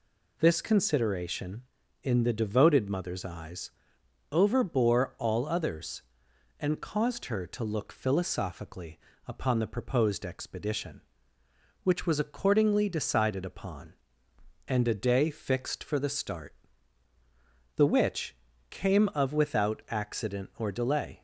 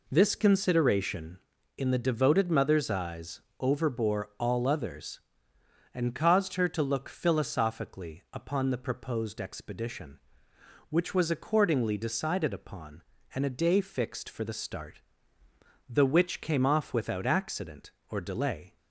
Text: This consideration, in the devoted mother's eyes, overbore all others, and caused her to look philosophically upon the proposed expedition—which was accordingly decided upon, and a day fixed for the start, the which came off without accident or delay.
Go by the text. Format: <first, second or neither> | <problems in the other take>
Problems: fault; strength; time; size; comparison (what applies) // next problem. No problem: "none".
second | pauses between "philosophically" and "upon"; slight; at 8.9 s; 0.28 s long // pauses between "which" and "came"; slight; at 18.3 s; 0.34 s long // says "of" for "off"; at 19.1 s